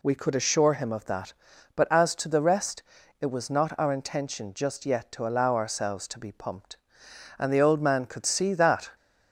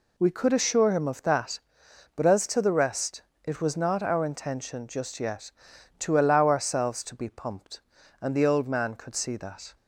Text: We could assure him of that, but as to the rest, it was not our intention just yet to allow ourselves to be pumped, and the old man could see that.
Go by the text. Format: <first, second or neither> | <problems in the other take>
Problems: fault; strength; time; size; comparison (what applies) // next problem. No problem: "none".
neither | none